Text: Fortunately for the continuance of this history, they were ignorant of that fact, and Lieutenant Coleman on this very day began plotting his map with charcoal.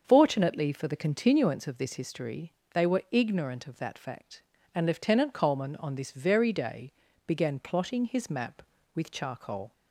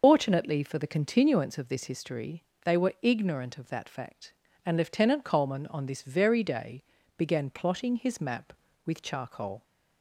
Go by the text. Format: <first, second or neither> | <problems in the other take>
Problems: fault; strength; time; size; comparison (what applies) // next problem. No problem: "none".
first | loses the start of "Fortunately"; at 0.0 s; 65 ms // starts louder than the rest; noticeable; until 1.0 s; 6 dB; also in the first // pauses between "day" and "began"; slight; at 6.8 s; 0.32 s long; slight in the first